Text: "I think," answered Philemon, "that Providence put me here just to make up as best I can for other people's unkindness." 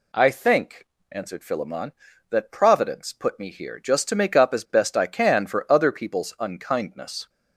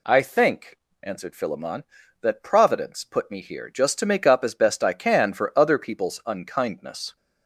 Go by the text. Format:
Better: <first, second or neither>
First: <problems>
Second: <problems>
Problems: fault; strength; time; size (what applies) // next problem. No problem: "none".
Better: neither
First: none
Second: none